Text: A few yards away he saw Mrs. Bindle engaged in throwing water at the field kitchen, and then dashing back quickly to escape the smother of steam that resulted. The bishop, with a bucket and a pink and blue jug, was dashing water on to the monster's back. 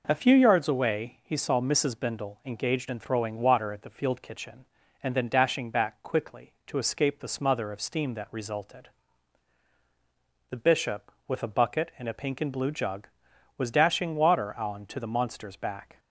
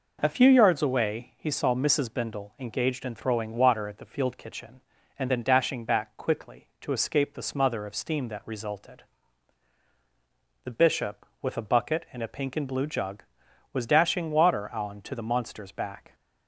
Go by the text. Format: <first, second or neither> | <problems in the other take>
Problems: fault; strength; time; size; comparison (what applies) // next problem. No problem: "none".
neither | none